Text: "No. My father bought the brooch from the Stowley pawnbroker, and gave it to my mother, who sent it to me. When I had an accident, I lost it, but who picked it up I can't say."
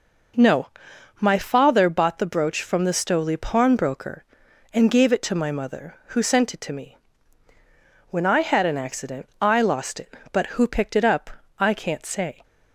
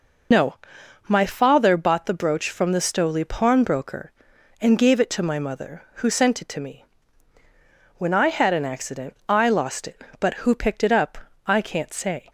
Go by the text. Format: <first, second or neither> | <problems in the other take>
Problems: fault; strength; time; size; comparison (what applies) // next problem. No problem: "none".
first | loses the start of "No"; at 0.3 s; 95 ms // pauses between "up" and "I"; slight; at 11.1 s; 0.26 s long; slight in the first